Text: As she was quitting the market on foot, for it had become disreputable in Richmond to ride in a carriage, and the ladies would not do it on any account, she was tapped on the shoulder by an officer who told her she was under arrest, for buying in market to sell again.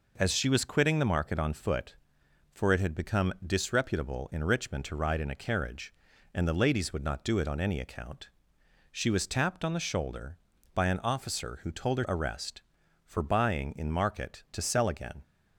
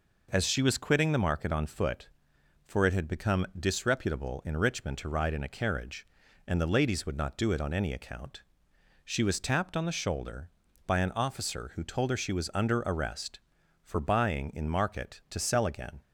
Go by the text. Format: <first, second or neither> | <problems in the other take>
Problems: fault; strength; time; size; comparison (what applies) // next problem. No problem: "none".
second | skips "she was under"; at 12.0 s